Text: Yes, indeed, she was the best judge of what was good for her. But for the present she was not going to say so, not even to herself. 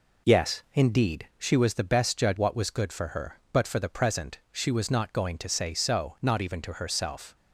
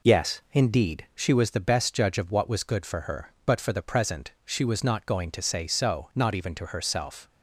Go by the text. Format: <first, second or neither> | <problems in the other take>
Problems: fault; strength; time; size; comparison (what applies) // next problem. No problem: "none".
second | skips "of"; at 2.3 s